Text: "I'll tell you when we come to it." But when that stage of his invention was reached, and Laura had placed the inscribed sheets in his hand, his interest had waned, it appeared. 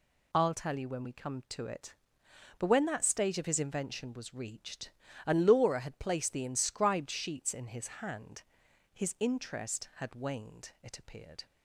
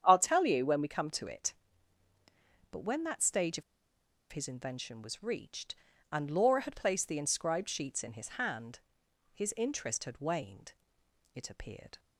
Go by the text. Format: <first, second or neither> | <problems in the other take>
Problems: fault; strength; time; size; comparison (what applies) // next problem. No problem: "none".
first | starts louder than the rest; strong; until 1.0 s; 8.5 dB // pauses between "of" and "his"; noticeable; at 3.6 s; 0.69 s long